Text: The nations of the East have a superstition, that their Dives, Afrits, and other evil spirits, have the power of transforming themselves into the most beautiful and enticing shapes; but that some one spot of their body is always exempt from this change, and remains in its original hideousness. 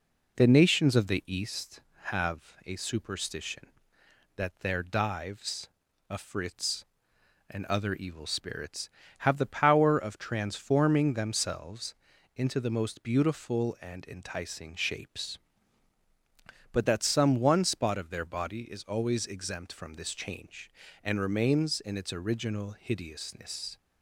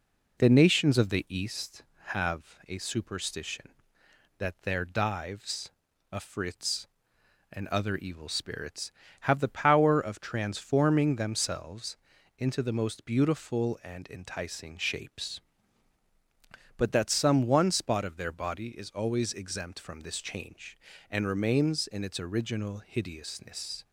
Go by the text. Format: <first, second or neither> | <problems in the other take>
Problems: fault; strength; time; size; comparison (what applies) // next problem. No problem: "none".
neither | pauses between "themselves" and "into"; the same in both